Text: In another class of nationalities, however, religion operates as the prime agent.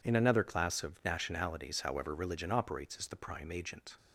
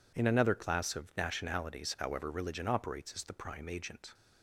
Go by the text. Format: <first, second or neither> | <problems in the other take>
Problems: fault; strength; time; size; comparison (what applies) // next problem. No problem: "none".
neither | none